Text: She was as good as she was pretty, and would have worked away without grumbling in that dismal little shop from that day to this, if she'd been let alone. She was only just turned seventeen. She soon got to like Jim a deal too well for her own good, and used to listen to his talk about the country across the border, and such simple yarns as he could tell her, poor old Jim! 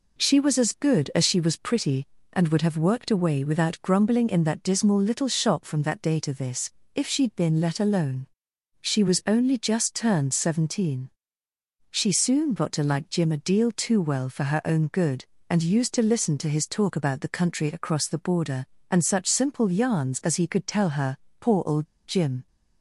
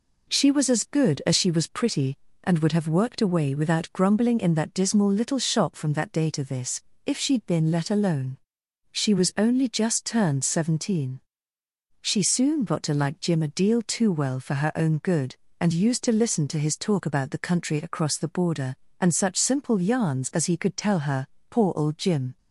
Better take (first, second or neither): second